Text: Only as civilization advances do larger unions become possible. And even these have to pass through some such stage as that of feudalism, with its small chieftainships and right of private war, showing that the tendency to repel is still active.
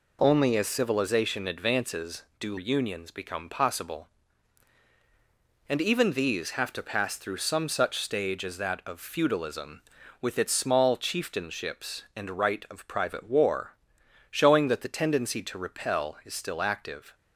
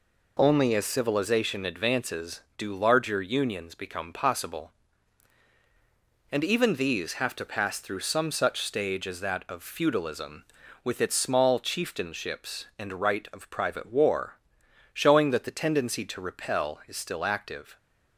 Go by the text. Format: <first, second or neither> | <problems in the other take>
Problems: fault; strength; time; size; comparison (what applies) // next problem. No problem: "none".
second | skips "larger"; at 2.5 s